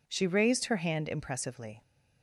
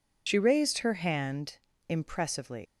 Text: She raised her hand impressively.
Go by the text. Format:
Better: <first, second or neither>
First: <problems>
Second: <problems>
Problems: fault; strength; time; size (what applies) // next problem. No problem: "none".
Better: first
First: none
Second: loses the start of "She"; at 0.2 s; 50 ms // pauses between "hand" and "impressively"; slight; at 1.5 s; 0.32 s long